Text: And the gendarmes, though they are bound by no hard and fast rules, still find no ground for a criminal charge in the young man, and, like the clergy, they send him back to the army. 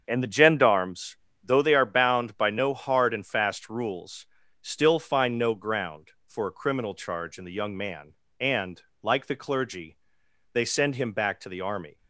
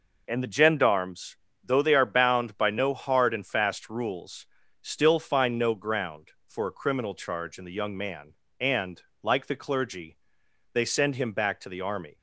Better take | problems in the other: second | starts louder than the rest; until 1.8 s; 7 dB

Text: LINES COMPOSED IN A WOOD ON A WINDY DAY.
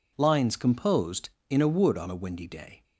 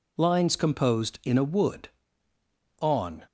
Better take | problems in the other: first | stops before "A WINDY DAY"; at 3.2 s

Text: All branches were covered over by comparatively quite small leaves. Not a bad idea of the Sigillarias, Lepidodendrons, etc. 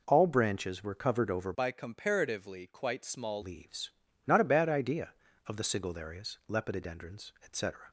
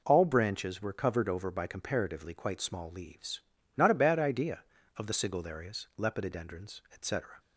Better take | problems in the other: second | changes voice from "by" to "small"; from 1.5 to 3.4 s; 1.9 s long

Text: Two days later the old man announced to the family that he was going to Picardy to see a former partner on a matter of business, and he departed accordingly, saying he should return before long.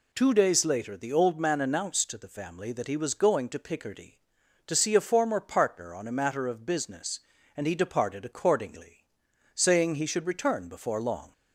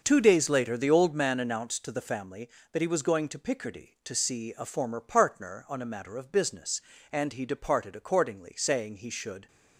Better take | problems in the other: first | starts louder than the rest; noticeable; until 1.0 s; 6 dB // stops before "return before long"; at 9.4 s

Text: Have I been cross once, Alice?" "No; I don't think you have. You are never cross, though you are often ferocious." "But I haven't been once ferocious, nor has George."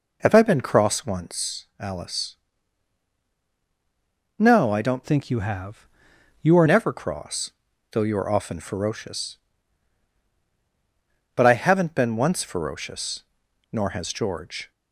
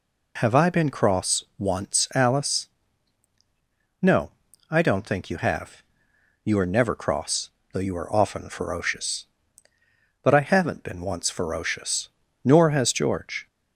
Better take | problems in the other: second | changes voice from "think" to "are"; from 5.0 to 6.6 s; 1.6 s long

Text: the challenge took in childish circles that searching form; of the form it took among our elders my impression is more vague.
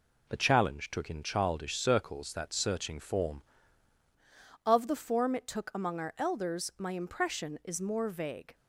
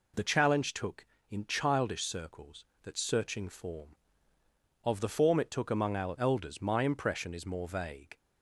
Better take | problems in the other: second | changes voice at "of"; from 4.6 s on; 3.9 s long

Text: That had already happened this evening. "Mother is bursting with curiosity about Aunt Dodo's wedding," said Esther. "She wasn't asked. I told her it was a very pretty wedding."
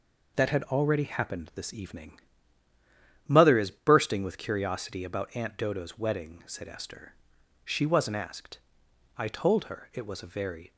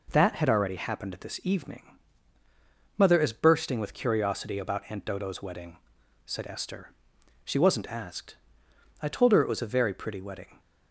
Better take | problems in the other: second | stops before "pretty wedding"; at 10.7 s

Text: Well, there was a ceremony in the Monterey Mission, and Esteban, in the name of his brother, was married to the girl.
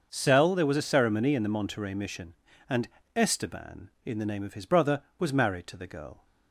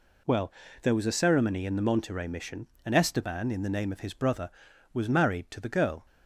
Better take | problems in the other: second | starts louder than the rest; until 1.1 s; 6 dB // says "Cell" for "Well"; at 0.1 s // pauses between "and" and "Esteban"; slight; at 2.8 s; 0.26 s long

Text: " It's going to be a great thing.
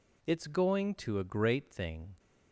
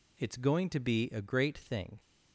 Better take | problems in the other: second | skips "be"; at 1.1 s

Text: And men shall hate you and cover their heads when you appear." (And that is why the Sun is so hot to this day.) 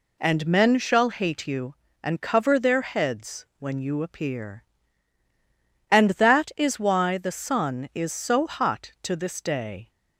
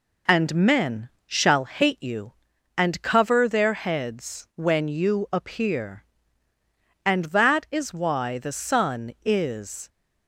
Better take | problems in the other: first | pauses between "men" and "shall"; slight; at 1.0 s; 0.18 s long // stops before "so hot to this day"; at 9.8 s

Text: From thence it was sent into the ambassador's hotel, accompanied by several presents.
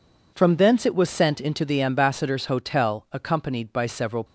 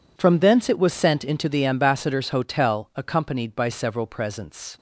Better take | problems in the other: second | stops before "presents"; at 4.2 s

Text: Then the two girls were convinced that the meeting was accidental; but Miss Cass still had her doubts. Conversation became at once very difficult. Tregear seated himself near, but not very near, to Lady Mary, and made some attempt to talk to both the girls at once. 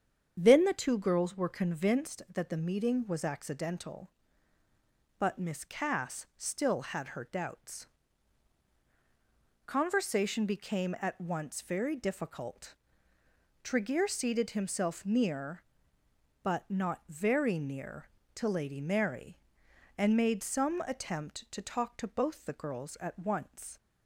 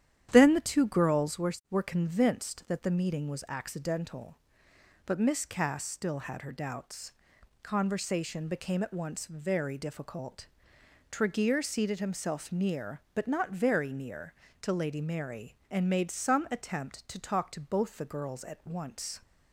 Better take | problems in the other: first | starts louder than the rest; strong; until 1.3 s; 10.5 dB; strong in the first // says "were" twice; at 1.7 s

